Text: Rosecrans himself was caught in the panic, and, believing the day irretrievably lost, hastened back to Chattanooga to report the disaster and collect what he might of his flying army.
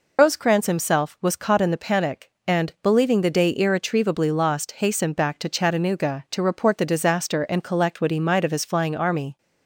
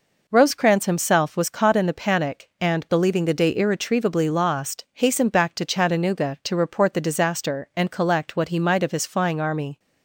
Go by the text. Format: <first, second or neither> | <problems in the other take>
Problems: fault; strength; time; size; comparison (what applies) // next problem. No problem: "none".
second | loses the start of "Rosecrans"; at 0.1 s; 135 ms